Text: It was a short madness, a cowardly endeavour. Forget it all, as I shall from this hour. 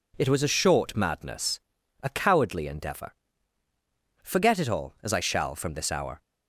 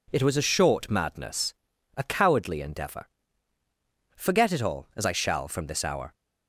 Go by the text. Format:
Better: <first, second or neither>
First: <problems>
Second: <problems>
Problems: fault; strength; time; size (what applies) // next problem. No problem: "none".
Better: neither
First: none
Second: none